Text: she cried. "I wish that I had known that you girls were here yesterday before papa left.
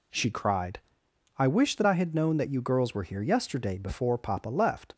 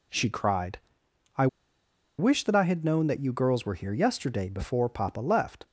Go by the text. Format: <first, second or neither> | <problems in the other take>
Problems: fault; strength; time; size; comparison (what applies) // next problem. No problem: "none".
first | pauses between "I" and "wish"; noticeable; at 1.4 s; 0.72 s long